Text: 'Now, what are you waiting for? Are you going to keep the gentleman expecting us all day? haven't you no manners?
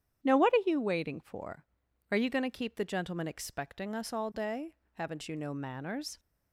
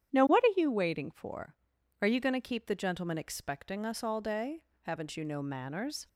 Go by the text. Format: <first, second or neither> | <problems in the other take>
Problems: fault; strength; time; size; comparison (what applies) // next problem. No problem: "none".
neither | starts louder than the rest; strong; the same in both